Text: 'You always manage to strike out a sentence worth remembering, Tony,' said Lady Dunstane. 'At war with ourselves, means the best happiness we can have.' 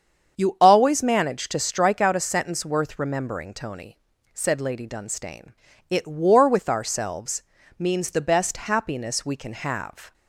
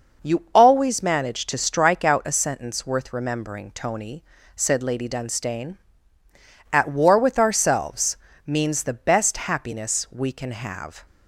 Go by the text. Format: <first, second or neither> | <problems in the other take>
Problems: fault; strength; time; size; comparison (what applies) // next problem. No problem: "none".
second | starts louder than the rest; strong; until 1.4 s; 7.5 dB // says "It" for "At"; at 5.8 s